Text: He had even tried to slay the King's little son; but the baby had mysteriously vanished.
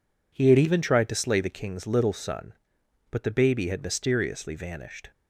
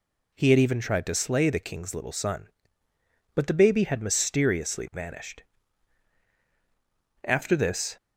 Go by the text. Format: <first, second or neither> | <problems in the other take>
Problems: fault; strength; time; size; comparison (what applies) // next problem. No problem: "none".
first | goes on to say "After this"; noticeable; from 7.2 s on; 0.72 s long